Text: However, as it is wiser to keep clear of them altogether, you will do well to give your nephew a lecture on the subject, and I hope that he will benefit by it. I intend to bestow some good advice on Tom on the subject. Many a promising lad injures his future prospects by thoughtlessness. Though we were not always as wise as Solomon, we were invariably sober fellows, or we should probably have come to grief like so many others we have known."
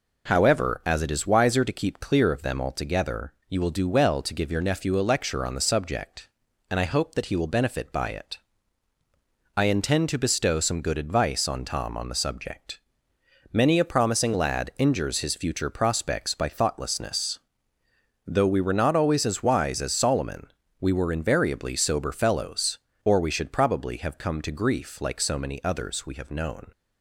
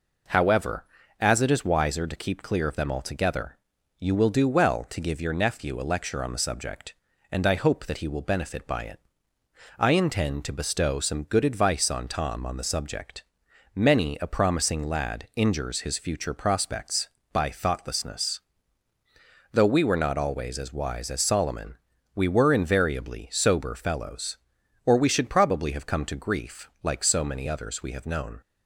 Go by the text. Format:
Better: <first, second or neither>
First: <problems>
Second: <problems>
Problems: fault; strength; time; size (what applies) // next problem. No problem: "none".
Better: neither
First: none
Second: none